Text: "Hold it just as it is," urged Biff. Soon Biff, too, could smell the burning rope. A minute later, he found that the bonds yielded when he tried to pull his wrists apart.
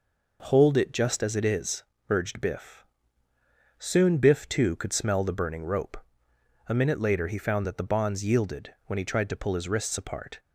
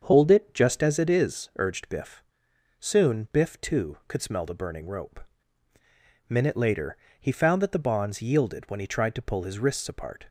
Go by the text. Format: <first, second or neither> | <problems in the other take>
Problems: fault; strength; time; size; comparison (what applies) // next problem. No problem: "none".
first | starts louder than the rest; until 1.0 s; 7 dB // skips "A"; at 5.7 s